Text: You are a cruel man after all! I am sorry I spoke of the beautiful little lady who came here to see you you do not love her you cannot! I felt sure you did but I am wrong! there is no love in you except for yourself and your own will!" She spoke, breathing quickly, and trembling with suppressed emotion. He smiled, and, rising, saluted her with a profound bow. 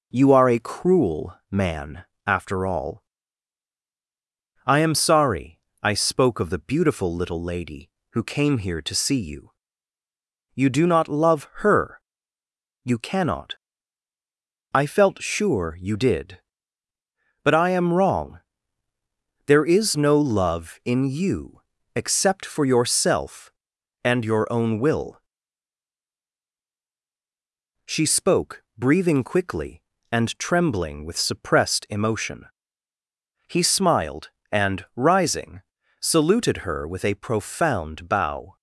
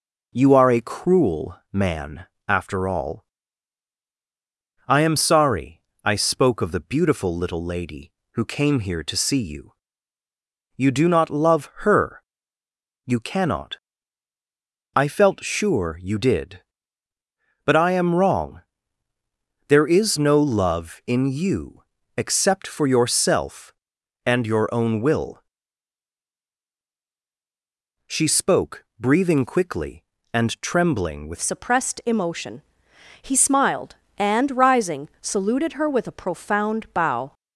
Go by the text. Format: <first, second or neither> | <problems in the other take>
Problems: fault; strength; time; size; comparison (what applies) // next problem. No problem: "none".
first | pauses between "man" and "after"; slight; at 2.2 s; 0.24 s long; slight in the first // pauses between "sorry" and "I"; slight; at 5.8 s; 0.20 s long; slight in the first // pauses between "you" and "you"; at 9.7 s; 1.0 s long; also in the first // pauses between "her" and "you"; noticeable; at 12.2 s; 0.82 s long; noticeable in the first // pauses between "you" and "except"; slight; at 21.8 s; 0.34 s long; slight in the first // changes voice at "suppressed"; from 31.3 s on; 6.0 s long